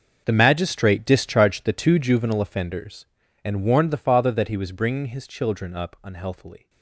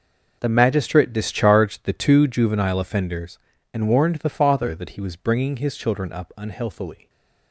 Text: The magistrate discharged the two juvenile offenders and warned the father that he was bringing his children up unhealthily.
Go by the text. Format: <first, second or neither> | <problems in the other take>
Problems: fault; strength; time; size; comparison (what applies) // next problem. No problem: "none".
second | gets quieter; strong; throughout; 17.5 dB